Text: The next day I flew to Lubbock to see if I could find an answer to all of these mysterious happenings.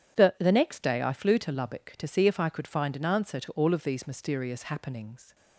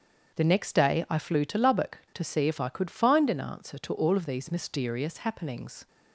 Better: second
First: starts louder than the rest; strong; until 1.2 s; 10 dB // says "The" twice; at 0.3 s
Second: starts louder than the rest; strong; until 1.4 s; 7.5 dB

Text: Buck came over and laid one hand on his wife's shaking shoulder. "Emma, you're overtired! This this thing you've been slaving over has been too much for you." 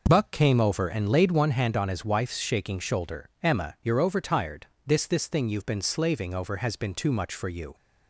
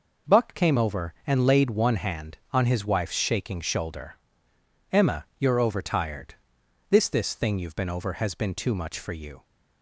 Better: first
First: none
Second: skips "slaving"; at 7.8 s

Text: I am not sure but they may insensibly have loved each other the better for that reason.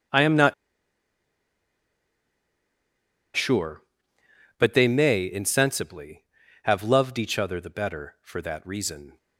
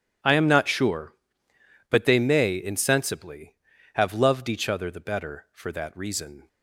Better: second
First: pauses between "not" and "sure"; strong; at 0.5 s; 2.8 s long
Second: none

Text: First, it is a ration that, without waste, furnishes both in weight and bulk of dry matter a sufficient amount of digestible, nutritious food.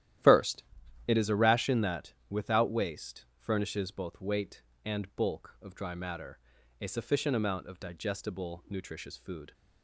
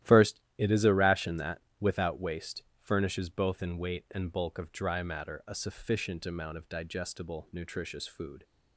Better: second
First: starts louder than the rest; strong; until 1.6 s; 12.5 dB // skips "in"; at 4.1 s // pauses between "matter" and "a"; at 6.3 s; 0.42 s long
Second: starts louder than the rest; strong; until 1.1 s; 13 dB

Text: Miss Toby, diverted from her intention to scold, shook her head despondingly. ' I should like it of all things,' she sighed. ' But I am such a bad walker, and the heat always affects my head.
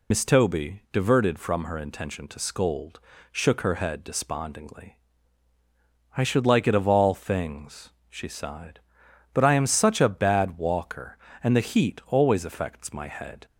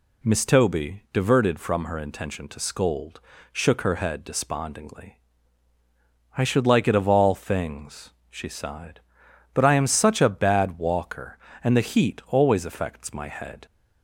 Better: second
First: loses the start of "Miss"; at 0.1 s; 75 ms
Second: none

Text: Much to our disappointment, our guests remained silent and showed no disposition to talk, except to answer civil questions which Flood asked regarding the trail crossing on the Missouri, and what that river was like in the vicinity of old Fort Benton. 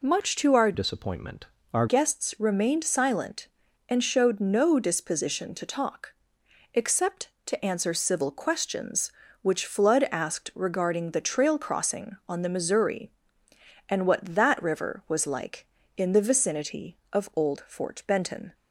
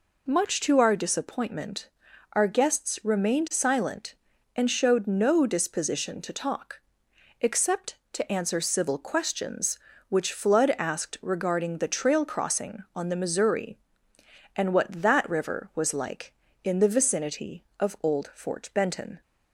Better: second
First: changes voice from "disappointment" to "our"; from 0.7 to 1.8 s; 1.1 s long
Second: none

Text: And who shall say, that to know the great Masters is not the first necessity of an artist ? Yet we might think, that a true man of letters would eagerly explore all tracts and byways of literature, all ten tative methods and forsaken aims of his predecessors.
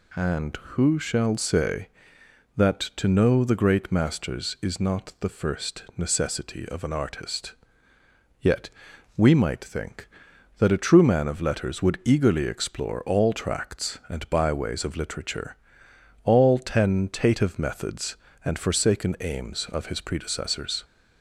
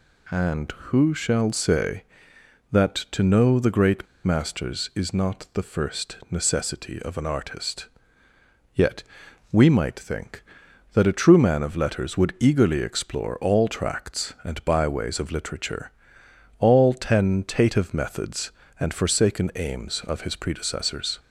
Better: first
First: pauses between "Yet" and "we"; noticeable; at 8.6 s; 0.48 s long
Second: pauses between "great" and "Masters"; slight; at 4.0 s; 0.18 s long // pauses between "Yet" and "we"; noticeable; at 9.0 s; 0.50 s long

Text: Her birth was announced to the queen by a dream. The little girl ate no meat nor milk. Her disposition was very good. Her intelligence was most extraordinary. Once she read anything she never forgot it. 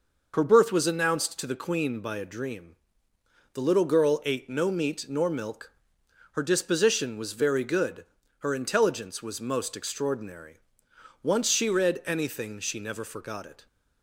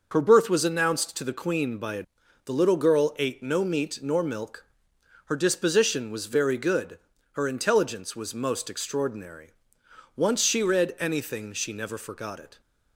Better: first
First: none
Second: starts louder than the rest; noticeable; until 1.1 s; 6 dB // skips "dream"; at 2.2 s

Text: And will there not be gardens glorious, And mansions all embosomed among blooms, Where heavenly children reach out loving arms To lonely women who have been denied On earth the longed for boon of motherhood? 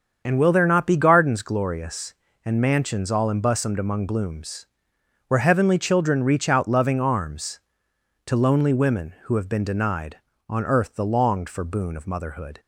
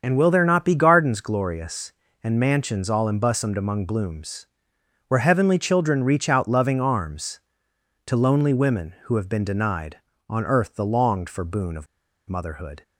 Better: first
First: starts louder than the rest; until 1.2 s; 7 dB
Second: starts louder than the rest; until 1.0 s; 7 dB // pauses between "of" and "motherhood"; at 11.8 s; 0.44 s long

